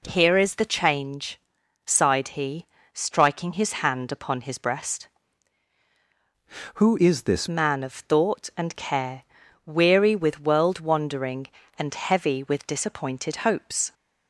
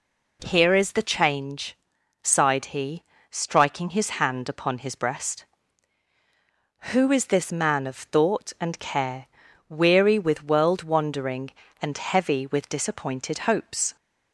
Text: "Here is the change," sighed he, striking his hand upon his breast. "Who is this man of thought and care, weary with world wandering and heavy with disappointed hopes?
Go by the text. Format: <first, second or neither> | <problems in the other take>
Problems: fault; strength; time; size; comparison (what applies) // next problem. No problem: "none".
second | changes voice from "Who" to "this"; from 6.7 to 7.4 s; 0.7 s long